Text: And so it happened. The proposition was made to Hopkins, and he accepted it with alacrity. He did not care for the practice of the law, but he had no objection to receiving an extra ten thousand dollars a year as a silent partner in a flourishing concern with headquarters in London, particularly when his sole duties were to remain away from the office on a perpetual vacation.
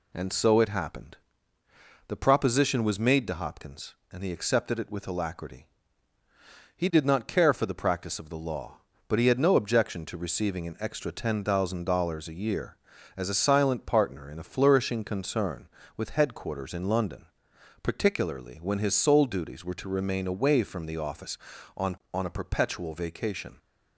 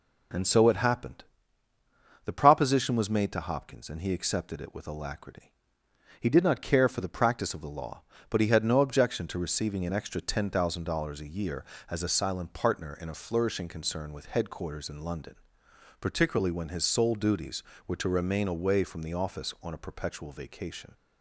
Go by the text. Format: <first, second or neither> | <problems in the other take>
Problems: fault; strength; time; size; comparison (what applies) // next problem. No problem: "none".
second | says "on" twice; at 22.1 s